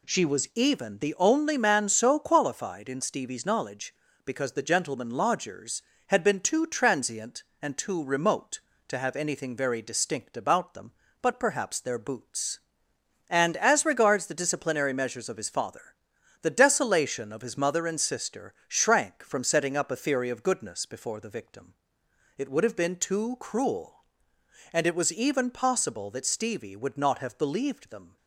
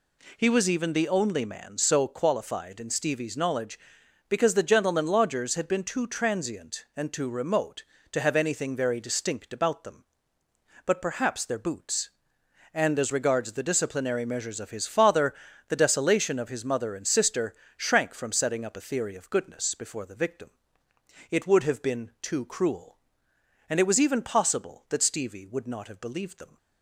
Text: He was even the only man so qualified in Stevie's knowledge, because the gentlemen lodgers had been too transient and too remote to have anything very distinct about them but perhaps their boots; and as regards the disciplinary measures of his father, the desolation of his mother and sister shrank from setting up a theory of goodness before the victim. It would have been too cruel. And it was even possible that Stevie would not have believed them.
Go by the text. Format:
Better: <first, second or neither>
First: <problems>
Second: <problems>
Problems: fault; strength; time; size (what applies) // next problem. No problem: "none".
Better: second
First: says "She" for "He"; at 0.0 s // pauses between "sister" and "shrank"; slight; at 18.5 s; 0.16 s long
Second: pauses between "sister" and "shrank"; slight; at 17.5 s; 0.24 s long